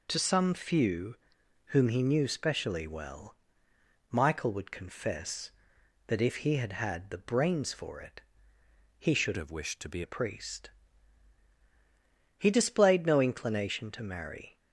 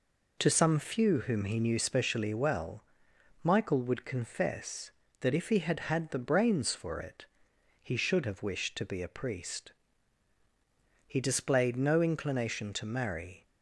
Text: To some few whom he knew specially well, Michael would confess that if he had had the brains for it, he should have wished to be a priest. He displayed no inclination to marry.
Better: second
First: pauses between "few" and "whom"; noticeable; at 1.1 s; 0.50 s long // changes voice from "have" to "be"; from 9.3 to 10.0 s; 0.7 s long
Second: none

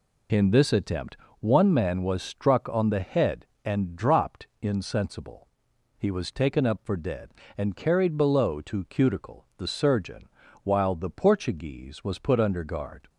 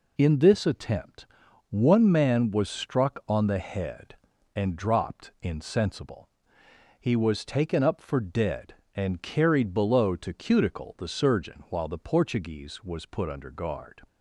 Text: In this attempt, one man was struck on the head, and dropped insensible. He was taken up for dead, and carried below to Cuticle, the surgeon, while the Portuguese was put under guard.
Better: neither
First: none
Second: none

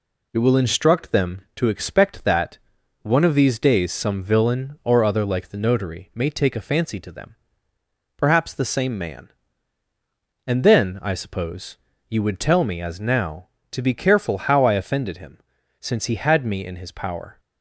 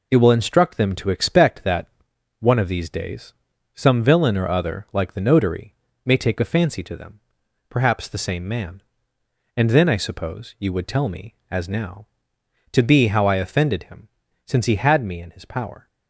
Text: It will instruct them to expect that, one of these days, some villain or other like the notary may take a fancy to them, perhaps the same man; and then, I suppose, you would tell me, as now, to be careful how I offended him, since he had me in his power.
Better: first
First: none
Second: pauses between "notary" and "may"; slight; at 5.7 s; 0.30 s long // skips "careful"; at 13.0 s

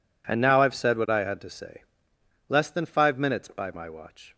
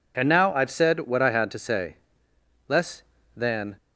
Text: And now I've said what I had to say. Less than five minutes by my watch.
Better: first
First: none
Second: stops before "five minutes by my watch"; at 3.7 s

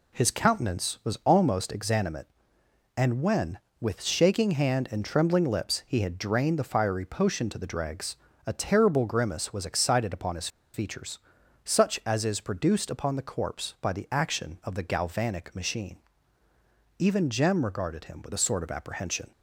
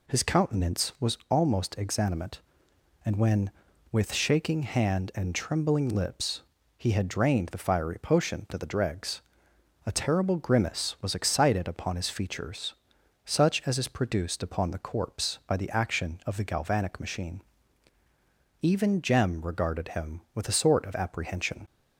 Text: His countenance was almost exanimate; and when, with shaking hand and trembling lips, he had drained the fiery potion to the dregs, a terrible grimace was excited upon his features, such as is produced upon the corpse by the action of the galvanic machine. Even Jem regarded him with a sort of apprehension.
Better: second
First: pauses between "his" and "features"; slight; at 10.4 s; 0.26 s long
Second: none

